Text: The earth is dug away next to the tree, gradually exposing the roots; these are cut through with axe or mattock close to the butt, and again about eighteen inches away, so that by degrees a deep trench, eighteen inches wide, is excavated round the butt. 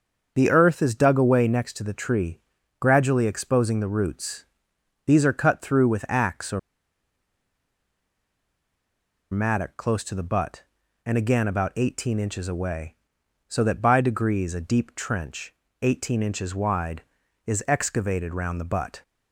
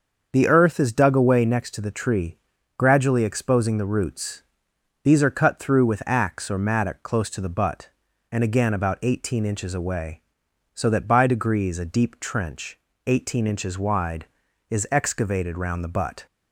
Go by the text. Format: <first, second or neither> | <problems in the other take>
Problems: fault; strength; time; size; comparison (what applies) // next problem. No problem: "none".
second | starts louder than the rest; until 1.3 s; 6.5 dB; also in the second // pauses between "or" and "mattock"; strong; at 6.5 s; 2.7 s long